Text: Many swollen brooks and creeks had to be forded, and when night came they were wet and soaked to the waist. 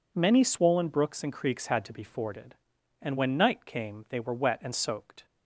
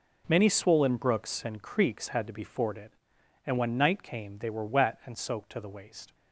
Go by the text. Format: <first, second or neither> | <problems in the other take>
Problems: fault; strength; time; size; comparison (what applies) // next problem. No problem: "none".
second | stops before "to the waist"; at 5.2 s